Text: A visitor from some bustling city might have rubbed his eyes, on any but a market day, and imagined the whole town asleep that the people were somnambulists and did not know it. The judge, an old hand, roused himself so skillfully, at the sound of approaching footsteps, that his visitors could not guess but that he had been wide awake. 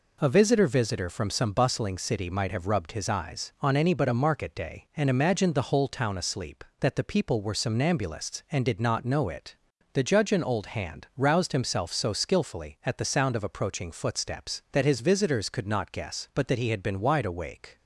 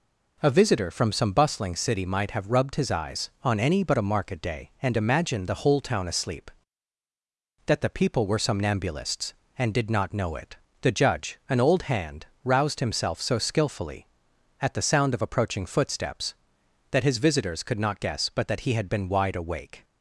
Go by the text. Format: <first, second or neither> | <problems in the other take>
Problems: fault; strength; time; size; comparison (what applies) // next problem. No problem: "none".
second | says "visitor" twice; at 0.6 s